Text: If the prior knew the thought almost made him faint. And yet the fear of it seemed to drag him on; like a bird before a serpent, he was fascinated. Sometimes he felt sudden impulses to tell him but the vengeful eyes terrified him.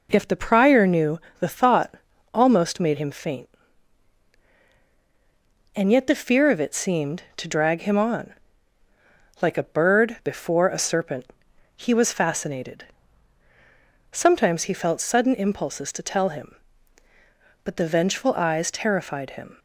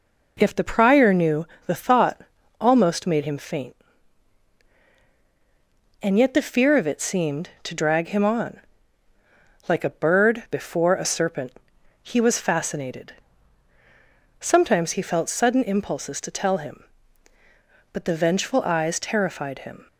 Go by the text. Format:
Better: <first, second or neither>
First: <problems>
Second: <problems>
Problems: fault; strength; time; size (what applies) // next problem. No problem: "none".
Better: neither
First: pauses between "knew" and "the"; slight; at 1.2 s; 0.18 s long // pauses between "thought" and "almost"; at 1.9 s; 0.40 s long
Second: pauses between "knew" and "the"; slight; at 1.4 s; 0.18 s long // pauses between "thought" and "almost"; at 2.2 s; 0.40 s long